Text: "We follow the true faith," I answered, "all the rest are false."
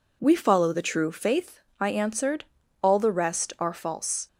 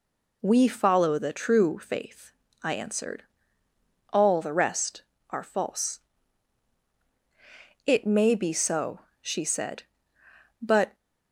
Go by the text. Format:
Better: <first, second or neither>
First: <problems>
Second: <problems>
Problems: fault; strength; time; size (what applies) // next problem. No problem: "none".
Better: first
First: none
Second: goes on to say "It may be so she said but"; strong; from 7.8 s on; 3.1 s long